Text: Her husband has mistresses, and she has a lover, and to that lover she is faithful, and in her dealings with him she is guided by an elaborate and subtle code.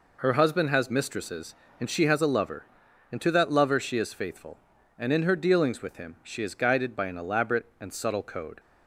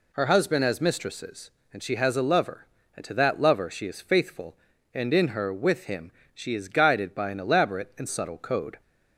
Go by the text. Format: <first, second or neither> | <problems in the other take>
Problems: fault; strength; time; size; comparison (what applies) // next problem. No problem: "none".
first | skips "dealings"; at 5.5 s // pauses between "him" and "she"; slight; at 6.1 s; 0.24 s long